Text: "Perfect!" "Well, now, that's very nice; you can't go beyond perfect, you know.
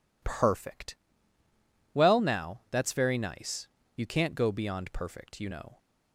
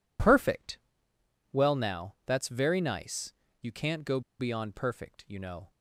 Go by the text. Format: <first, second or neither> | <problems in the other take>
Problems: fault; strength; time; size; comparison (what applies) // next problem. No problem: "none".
first | pauses between "go" and "beyond"; slight; at 4.2 s; 0.18 s long